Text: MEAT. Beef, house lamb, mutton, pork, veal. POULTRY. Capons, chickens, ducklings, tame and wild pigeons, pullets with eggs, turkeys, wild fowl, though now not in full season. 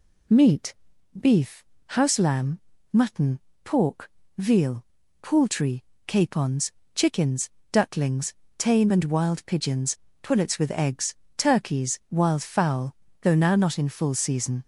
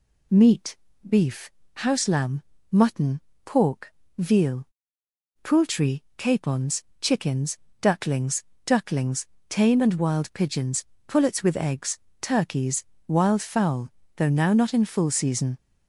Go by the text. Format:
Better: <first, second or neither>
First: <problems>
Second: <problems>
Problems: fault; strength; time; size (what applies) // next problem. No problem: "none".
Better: first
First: none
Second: says "ducklings" twice; at 8.6 s